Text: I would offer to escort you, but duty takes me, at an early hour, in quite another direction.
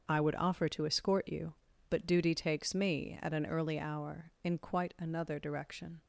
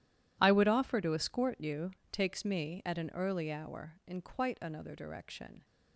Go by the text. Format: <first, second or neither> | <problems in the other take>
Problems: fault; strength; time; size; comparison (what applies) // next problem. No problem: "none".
first | skips "but duty"; at 2.0 s